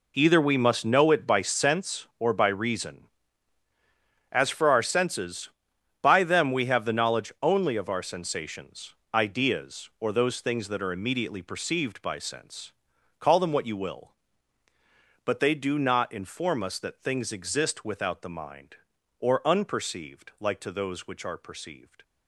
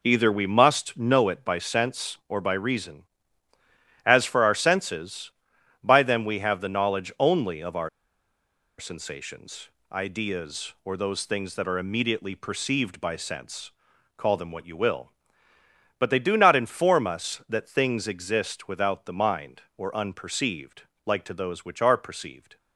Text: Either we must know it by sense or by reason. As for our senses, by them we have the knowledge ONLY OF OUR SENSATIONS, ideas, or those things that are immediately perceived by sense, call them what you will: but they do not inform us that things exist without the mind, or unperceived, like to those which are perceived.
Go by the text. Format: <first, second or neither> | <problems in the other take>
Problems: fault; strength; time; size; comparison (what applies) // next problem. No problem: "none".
first | pauses between "OUR" and "SENSATIONS"; noticeable; at 7.8 s; 0.89 s long